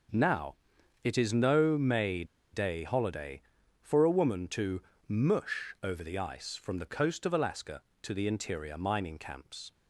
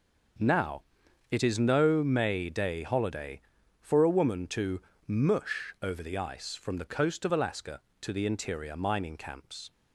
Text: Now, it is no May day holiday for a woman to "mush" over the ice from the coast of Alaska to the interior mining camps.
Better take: second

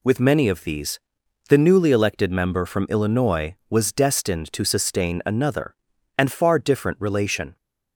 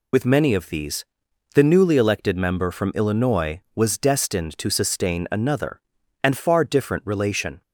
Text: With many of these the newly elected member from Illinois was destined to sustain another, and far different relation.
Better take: first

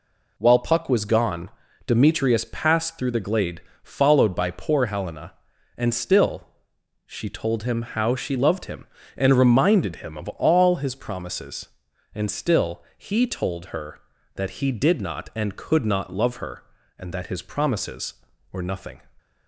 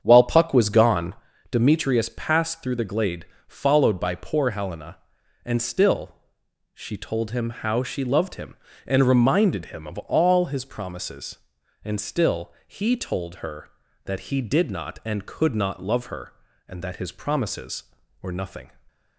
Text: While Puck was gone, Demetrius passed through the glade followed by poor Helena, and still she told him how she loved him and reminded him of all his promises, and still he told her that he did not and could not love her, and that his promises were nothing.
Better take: first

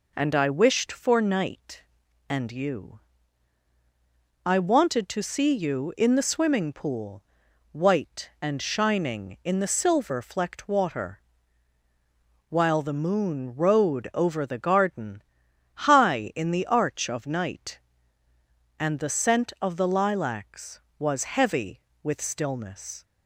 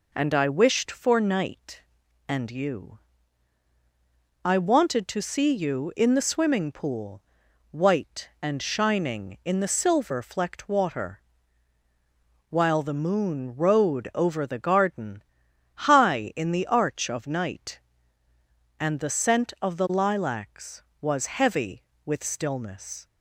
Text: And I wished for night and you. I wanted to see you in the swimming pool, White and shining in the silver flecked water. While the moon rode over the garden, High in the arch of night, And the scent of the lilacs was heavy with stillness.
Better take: neither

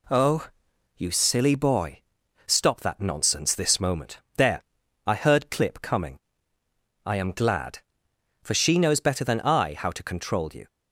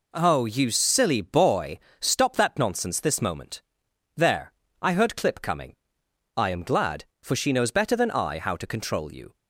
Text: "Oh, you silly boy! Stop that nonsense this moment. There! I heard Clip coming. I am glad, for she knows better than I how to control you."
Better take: neither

